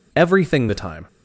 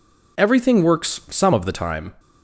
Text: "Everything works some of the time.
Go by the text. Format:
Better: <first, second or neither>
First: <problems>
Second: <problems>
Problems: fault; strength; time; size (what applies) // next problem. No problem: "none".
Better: second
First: skips "works some of"; at 0.6 s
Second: none